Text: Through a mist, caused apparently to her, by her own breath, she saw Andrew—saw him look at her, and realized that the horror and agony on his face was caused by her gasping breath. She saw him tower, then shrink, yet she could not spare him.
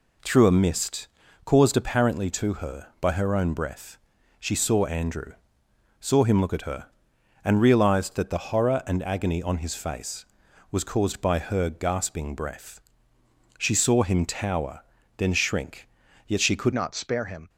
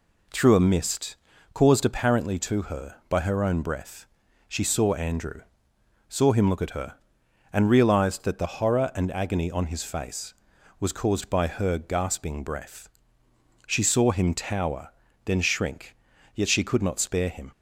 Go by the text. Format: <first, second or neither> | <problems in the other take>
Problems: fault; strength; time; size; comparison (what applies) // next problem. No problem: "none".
second | changes voice at "not"; from 16.7 s on; 0.7 s long